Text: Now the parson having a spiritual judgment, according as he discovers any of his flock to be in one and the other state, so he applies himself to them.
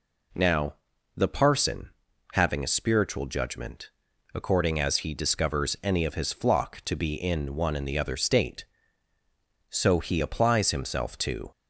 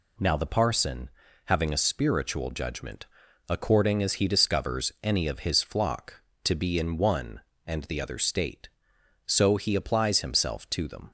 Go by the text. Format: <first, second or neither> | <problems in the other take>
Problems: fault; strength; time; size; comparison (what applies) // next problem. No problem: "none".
second | pauses between "Now" and "the"; at 0.7 s; 0.42 s long // pauses between "parson" and "having"; at 1.8 s; 0.44 s long; slight in the second // stops before "them"; at 11.5 s